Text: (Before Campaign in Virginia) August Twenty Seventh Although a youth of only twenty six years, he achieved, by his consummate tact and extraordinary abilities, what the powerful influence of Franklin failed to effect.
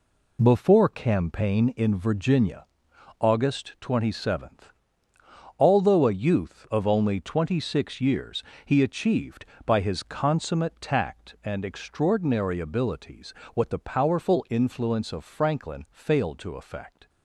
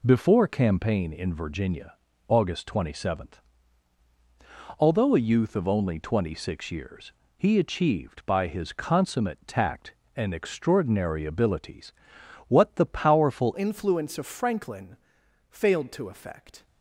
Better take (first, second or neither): first